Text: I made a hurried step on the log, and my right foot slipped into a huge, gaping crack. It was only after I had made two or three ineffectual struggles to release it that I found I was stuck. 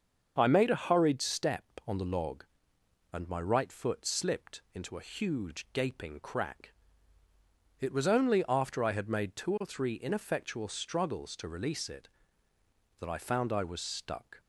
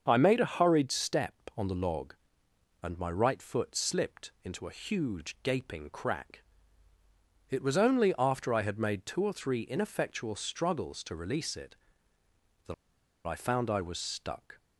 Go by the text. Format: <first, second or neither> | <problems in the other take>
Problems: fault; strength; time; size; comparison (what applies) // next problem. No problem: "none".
first | starts louder than the rest; until 1.0 s; 6.5 dB; also in the first // pauses between "that" and "I"; noticeable; at 12.7 s; 0.52 s long